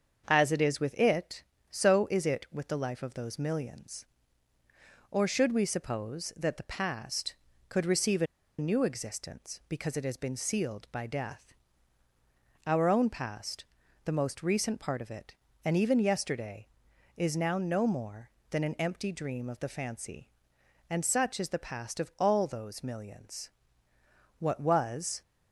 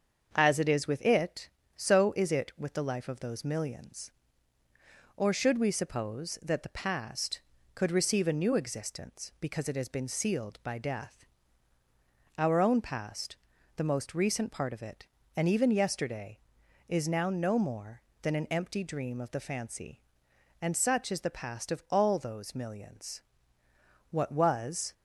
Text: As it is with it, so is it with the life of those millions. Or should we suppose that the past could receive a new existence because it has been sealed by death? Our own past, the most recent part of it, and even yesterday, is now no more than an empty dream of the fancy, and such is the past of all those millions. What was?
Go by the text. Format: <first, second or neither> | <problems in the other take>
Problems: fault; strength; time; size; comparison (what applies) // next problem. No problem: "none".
second | starts louder than the rest; until 1.2 s; 7 dB; also in the second // pauses between "a" and "new"; slight; at 8.2 s; 0.33 s long